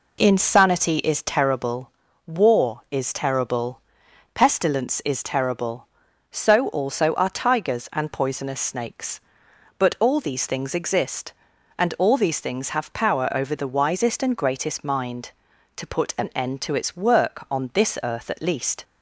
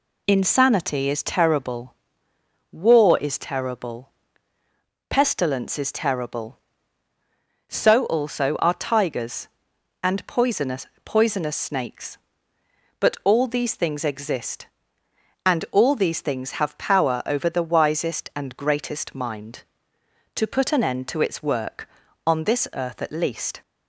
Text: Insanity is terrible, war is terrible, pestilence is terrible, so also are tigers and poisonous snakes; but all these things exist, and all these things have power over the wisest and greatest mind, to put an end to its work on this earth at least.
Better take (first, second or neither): first